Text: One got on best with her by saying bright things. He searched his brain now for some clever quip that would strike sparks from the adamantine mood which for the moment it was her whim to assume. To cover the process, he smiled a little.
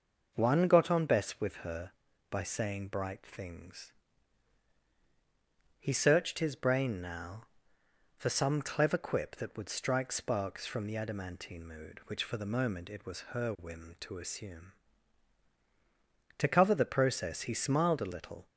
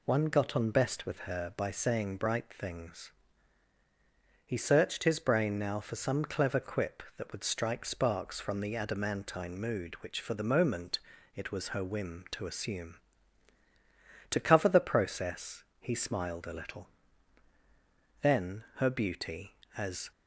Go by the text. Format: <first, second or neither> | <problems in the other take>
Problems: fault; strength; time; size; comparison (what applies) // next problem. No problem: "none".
first | pauses between "moment" and "it"; slight; at 10.9 s; 0.36 s long // goes on to say "Then her beauty as"; strong; from 18.2 s on; 1.9 s long